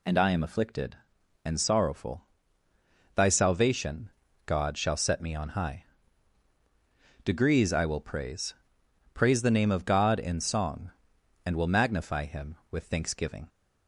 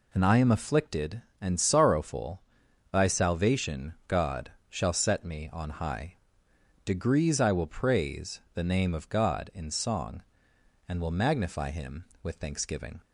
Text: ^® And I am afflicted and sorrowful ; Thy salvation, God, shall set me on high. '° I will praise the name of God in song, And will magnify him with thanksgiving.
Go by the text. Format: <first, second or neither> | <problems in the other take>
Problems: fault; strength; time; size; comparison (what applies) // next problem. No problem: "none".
second | says "praise" twice; at 9.1 s